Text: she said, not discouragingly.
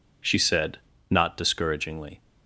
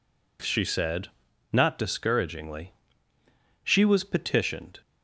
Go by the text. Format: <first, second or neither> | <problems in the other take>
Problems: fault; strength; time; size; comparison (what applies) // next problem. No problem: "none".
first | goes on to say "She was petitioned"; noticeable; from 3.6 s on; 1.1 s long